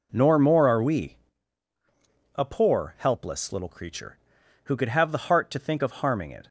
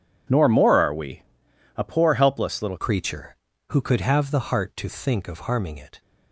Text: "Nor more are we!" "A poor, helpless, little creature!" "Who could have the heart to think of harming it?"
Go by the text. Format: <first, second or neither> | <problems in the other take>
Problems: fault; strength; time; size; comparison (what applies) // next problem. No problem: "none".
first | changes voice at "creature"; from 2.7 s on; 3.3 s long